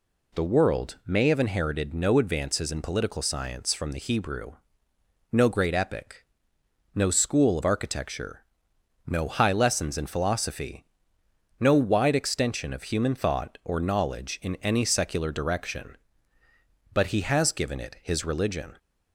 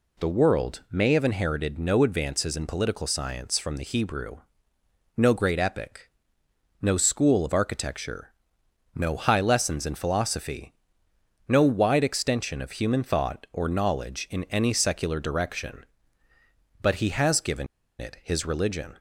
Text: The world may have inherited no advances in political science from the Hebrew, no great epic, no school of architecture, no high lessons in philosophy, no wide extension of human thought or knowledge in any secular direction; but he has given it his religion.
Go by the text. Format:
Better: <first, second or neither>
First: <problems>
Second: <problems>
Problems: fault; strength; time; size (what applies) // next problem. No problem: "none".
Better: first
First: none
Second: pauses between "given" and "it"; slight; at 17.6 s; 0.35 s long